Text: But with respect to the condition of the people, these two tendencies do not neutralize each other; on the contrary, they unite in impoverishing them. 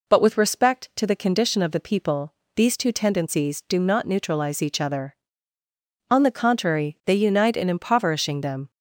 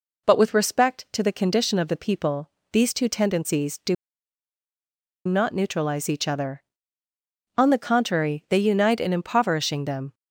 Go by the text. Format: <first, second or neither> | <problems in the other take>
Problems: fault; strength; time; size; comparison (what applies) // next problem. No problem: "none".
first | pauses between "do" and "not"; strong; at 3.9 s; 1.3 s long